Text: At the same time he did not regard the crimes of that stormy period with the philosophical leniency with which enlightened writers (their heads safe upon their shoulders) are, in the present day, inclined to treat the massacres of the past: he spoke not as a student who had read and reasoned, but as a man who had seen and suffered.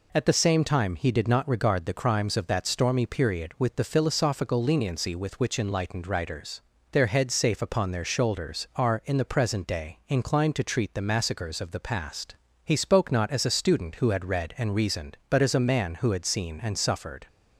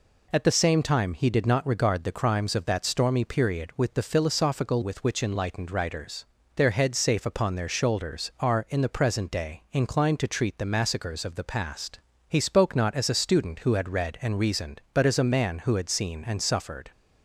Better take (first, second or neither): first